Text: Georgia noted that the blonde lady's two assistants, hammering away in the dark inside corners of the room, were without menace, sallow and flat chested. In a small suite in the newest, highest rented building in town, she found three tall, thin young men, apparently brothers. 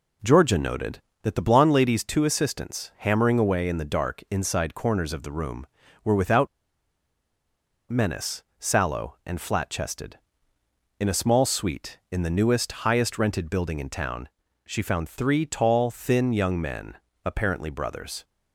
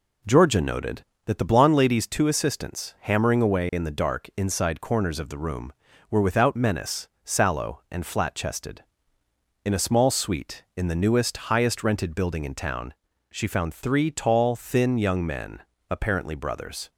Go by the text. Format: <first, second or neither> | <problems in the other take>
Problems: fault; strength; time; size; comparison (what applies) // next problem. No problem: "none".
second | pauses between "without" and "menace"; strong; at 6.4 s; 1.4 s long